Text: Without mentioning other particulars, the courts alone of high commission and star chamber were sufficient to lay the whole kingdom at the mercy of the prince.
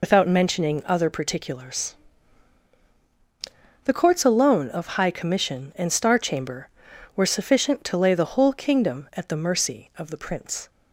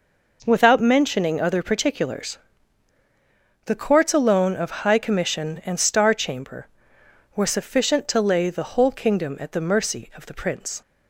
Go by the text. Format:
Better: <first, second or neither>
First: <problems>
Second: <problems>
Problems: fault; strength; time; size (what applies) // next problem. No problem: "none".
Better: second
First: loses the start of "Without"; at 0.0 s; 115 ms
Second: none